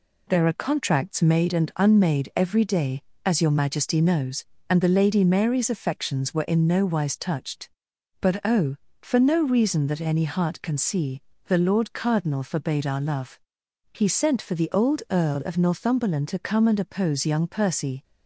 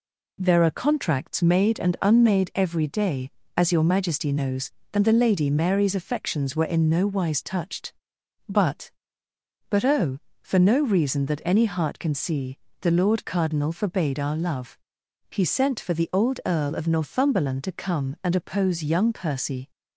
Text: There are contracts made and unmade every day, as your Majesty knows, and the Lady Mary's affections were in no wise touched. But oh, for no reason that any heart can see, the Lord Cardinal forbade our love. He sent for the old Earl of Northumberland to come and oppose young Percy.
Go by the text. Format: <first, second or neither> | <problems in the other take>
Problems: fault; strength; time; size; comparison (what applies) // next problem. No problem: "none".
first | says "But" twice; at 9.6 s